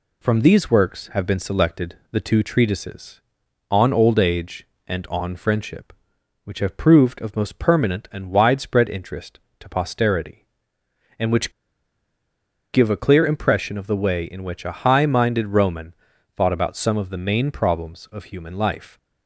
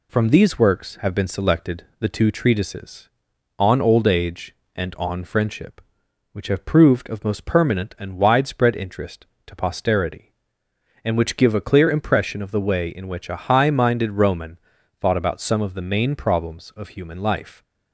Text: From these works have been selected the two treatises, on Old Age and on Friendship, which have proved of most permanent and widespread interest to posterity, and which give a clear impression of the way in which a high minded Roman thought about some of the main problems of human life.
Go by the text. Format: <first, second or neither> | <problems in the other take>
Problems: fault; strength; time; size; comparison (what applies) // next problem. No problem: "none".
second | pauses between "selected" and "the"; slight; at 1.9 s; 0.16 s long; slight in the second // pauses between "which" and "give"; at 11.5 s; 1.2 s long // pauses between "Roman" and "thought"; at 15.9 s; 0.44 s long; also in the second